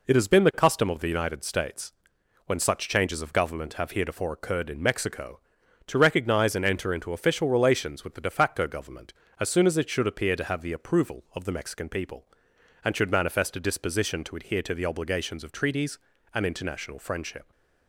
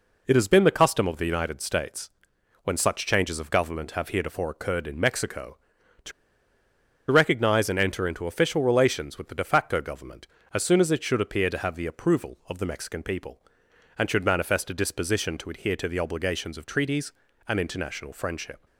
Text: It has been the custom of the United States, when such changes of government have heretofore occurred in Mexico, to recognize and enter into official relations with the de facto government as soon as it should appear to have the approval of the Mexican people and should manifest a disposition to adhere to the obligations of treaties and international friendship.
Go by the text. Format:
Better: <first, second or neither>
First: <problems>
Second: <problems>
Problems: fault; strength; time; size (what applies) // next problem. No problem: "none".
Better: first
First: none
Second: pauses between "to" and "recognize"; at 6.1 s; 0.99 s long